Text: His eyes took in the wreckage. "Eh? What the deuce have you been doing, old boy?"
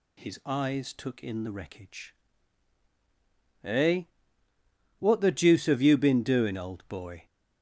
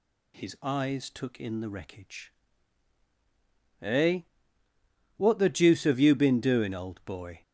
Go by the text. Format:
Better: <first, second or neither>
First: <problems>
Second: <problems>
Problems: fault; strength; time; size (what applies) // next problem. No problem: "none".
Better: neither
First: none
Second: none